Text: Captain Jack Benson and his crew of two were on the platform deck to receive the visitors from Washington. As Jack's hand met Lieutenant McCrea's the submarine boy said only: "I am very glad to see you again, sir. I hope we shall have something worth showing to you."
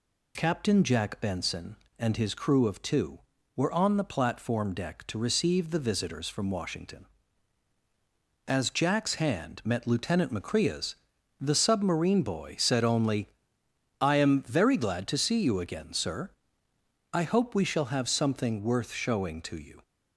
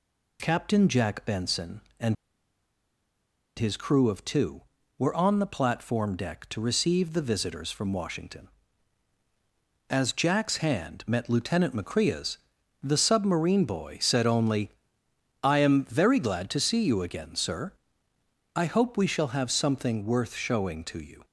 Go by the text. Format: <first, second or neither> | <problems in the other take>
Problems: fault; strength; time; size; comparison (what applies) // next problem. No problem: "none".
first | pauses between "and" and "his"; strong; at 2.1 s; 1.4 s long // pauses between "McCrea's" and "the"; noticeable; at 12.3 s; 0.46 s long; noticeable in the first